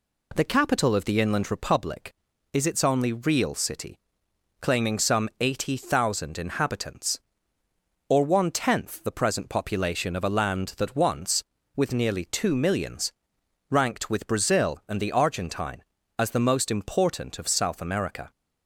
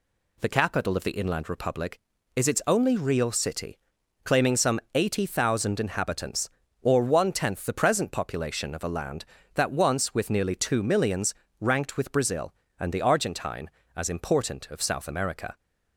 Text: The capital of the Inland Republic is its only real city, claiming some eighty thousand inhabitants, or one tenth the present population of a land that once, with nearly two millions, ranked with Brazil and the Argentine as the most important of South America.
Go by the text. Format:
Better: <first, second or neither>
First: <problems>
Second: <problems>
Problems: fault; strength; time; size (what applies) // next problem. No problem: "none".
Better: first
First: none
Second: pauses between "some" and "eighty"; slight; at 4.7 s; 0.16 s long // skips "the most"; at 14.0 s